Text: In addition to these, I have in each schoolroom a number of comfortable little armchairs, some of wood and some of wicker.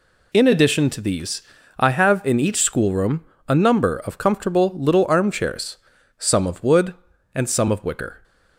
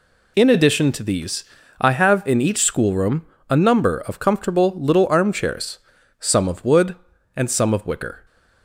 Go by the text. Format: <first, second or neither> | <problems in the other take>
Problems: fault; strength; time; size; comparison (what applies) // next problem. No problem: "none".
neither | pauses between "schoolroom" and "a"; slight; the same in both